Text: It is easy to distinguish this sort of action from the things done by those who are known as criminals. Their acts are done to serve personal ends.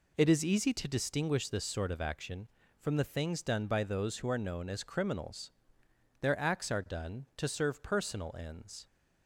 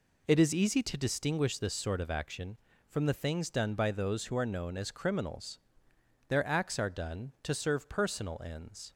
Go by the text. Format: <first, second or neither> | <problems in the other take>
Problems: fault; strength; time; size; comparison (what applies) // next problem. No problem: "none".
neither | none